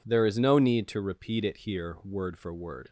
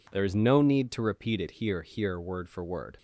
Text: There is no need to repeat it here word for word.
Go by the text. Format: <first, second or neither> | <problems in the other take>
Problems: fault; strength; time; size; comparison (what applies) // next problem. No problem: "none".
first | says "here" twice; at 1.8 s